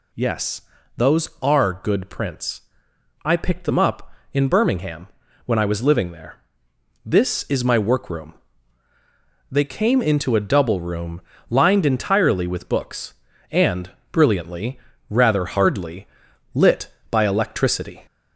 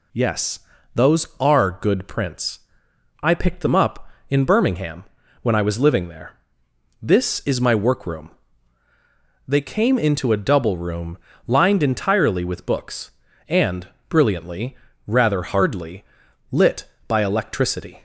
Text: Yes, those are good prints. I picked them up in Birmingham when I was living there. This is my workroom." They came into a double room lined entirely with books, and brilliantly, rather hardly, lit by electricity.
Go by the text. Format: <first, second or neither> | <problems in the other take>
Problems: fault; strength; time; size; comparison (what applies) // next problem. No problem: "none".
second | gets louder; slight; throughout; 2.5 dB // pauses between "Birmingham" and "when"; at 5.0 s; 0.38 s long; also in the second // pauses between "room" and "lined"; slight; at 11.2 s; 0.29 s long; slight in the second // pauses between "and" and "brilliantly"; slight; at 13.8 s; 0.22 s long; slight in the second